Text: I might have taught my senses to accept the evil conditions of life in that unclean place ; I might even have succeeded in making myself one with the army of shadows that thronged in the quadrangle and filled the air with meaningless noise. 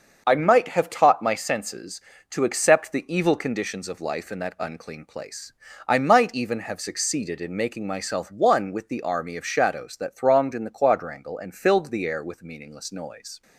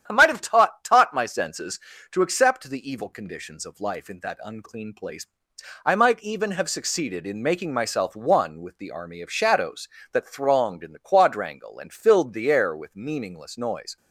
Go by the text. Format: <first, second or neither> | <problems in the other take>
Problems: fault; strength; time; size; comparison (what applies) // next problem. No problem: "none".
first | starts louder than the rest; strong; until 1.0 s; 9.5 dB; also in the first // says "taught" twice; at 0.8 s